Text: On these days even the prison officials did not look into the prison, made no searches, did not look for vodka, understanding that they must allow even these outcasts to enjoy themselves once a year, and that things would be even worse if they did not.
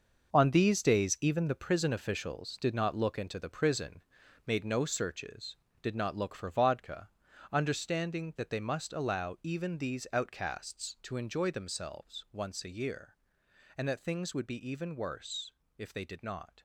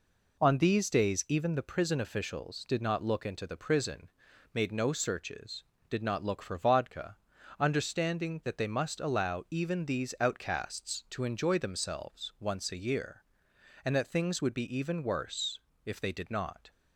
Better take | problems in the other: second | gets quieter; strong; throughout; 10.5 dB // pauses between "worse" and "if"; slight; at 15.5 s; 0.26 s long; slight in the second

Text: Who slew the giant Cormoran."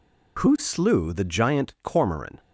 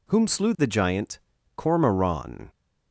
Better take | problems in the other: first | says "Whom" for "Who"; at 0.0 s // pauses between "giant" and "Cormoran"; slight; at 1.1 s; 0.36 s long

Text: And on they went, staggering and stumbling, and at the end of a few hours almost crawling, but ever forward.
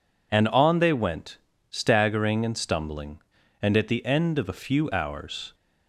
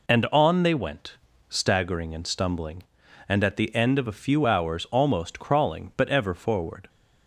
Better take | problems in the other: second | stops before "almost crawling but ever forward"; at 5.5 s

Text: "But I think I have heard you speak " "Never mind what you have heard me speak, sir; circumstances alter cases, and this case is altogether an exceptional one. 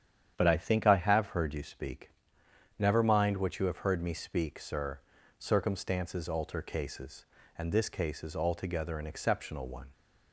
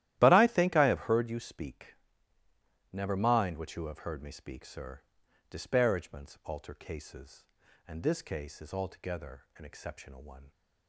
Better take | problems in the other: first | starts louder than the rest; strong; until 1.1 s; 13.5 dB; strong in the first // says "disparagements" for "circumstances"; at 5.4 s

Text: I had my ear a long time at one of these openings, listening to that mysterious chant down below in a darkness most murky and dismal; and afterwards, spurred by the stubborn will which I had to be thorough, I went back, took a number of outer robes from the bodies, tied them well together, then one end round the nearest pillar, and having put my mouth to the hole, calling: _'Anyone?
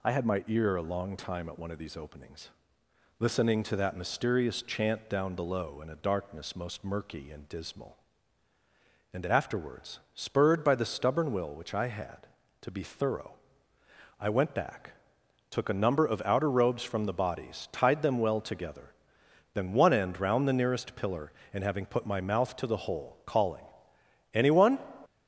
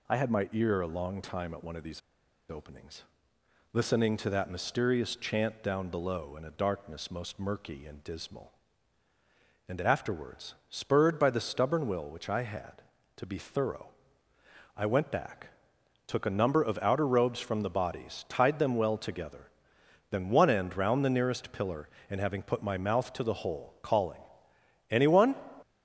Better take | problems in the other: first | pauses between "these" and "openings"; noticeable; at 2.0 s; 0.49 s long

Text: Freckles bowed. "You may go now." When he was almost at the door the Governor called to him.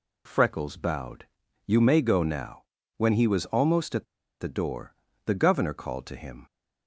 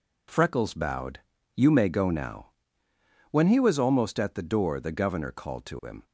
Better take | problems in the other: second | pauses between "at" and "the"; at 4.0 s; 0.36 s long // pauses between "door" and "the"; slight; at 4.9 s; 0.32 s long

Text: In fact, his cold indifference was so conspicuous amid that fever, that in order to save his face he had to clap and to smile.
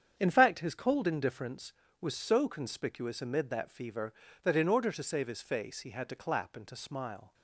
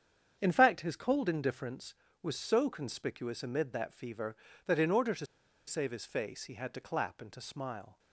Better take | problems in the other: first | starts louder than the rest; strong; until 1.4 s; 8 dB; strong in the first // pauses between "to" and "save"; at 5.2 s; 0.41 s long

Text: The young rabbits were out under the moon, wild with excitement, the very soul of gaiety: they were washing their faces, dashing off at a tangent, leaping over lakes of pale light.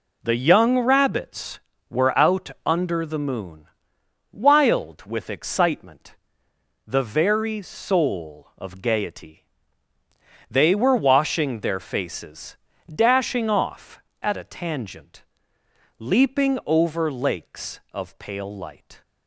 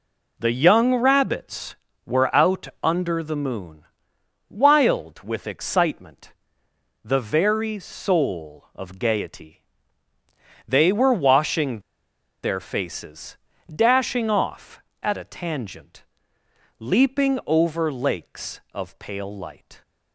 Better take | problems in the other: first | pauses between "out" and "under"; slight; at 2.6 s; 0.16 s long; slight in the first // pauses between "washing" and "their"; noticeable; at 11.7 s; 0.63 s long

